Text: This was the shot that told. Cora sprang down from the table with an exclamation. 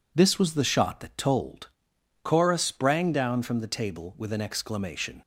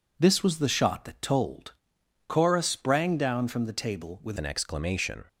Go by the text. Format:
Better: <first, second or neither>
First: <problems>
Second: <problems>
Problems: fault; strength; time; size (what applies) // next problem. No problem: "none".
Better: first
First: none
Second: changes voice at "an"; from 4.3 s on; 0.9 s long